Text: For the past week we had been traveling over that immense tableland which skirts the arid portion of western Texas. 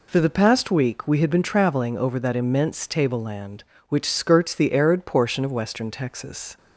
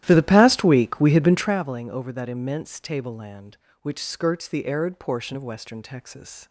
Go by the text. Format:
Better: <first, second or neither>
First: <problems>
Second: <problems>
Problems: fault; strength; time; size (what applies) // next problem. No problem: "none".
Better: first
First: none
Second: starts louder than the rest; strong; until 1.5 s; 13 dB